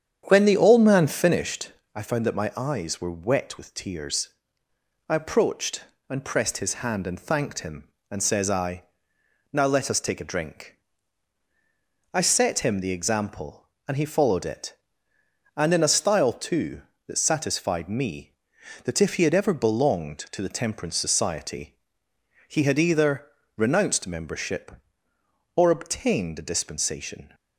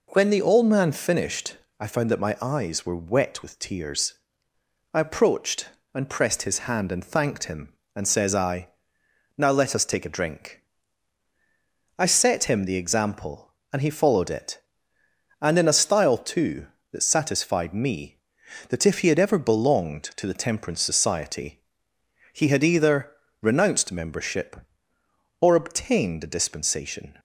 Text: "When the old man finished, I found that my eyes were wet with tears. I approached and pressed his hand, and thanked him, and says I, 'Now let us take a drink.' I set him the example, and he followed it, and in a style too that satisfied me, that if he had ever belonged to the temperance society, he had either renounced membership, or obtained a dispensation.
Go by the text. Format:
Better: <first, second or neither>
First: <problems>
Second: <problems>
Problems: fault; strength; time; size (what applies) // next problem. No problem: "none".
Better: second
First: starts louder than the rest; strong; until 1.6 s; 8.5 dB // pauses between "either" and "renounced"; slight; at 23.2 s; 0.30 s long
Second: pauses between "either" and "renounced"; slight; at 23.1 s; 0.30 s long